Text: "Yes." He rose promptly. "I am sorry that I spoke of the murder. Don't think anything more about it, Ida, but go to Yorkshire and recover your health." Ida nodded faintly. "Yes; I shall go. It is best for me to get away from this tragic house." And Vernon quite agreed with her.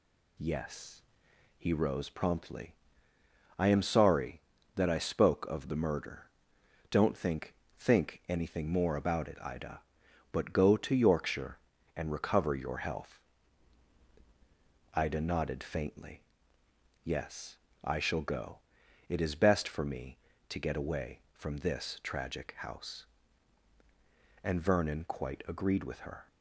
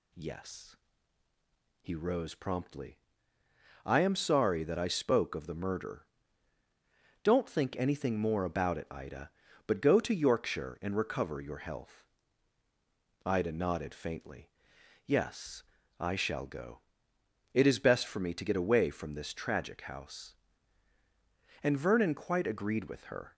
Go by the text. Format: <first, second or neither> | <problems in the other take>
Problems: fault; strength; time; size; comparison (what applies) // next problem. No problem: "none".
second | says "think" twice; at 7.7 s